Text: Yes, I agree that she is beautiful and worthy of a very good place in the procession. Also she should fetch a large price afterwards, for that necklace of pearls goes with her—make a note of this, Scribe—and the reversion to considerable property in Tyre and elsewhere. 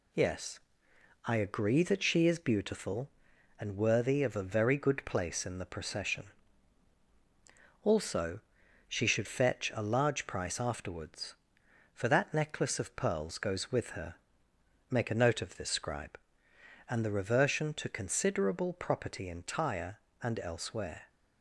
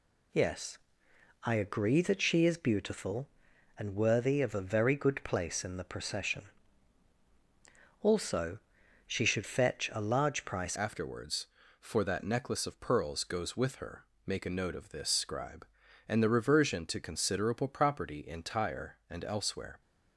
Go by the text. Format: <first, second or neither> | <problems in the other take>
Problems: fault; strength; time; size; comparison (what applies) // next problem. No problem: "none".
first | pauses between "Also" and "she"; noticeable; at 8.5 s; 0.50 s long; noticeable in the first // changes voice at "afterwards"; from 10.7 s on; 9.1 s long